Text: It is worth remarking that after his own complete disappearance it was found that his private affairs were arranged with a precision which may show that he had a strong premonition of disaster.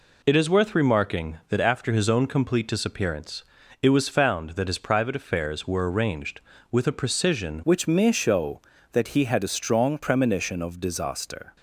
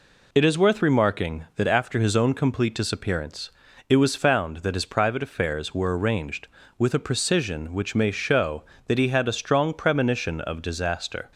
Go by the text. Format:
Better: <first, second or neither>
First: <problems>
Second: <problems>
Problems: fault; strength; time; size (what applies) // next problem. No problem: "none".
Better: second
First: pauses between "disappearance" and "it"; at 3.4 s; 0.40 s long // changes voice at "which"; from 7.6 s on; 3.9 s long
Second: pauses between "disappearance" and "it"; at 3.4 s; 0.40 s long